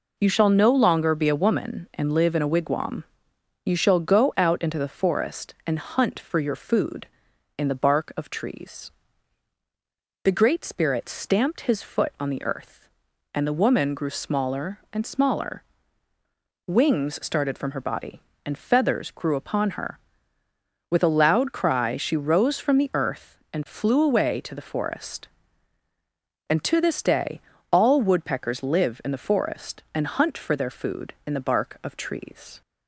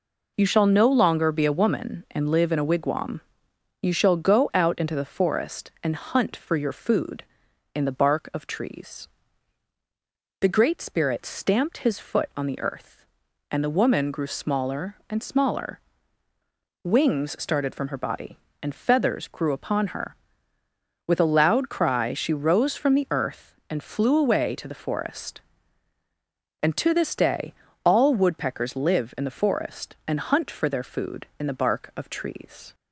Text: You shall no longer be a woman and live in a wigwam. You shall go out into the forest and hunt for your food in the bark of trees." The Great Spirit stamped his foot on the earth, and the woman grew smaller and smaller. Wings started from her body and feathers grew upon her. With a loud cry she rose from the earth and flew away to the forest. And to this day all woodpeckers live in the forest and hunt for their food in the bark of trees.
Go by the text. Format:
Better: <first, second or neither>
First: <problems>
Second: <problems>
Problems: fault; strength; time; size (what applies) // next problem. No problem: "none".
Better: neither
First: pauses between "day" and "all"; slight; at 27.4 s; 0.30 s long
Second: pauses between "day" and "all"; slight; at 27.5 s; 0.30 s long